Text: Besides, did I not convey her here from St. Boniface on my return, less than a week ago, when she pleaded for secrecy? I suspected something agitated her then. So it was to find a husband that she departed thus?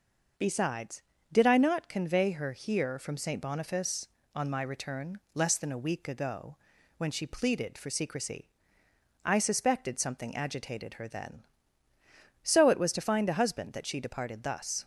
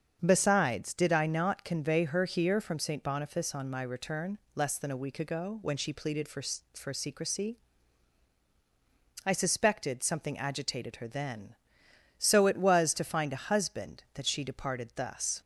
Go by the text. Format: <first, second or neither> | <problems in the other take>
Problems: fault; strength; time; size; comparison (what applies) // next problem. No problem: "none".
first | starts louder than the rest; until 1.2 s; 7 dB // says "for" twice; at 6.7 s